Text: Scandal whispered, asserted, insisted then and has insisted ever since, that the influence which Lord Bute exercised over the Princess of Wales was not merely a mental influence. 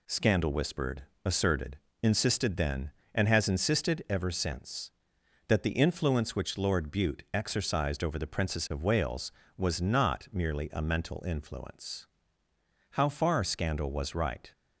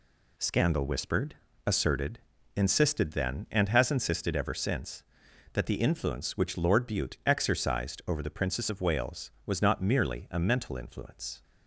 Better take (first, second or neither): second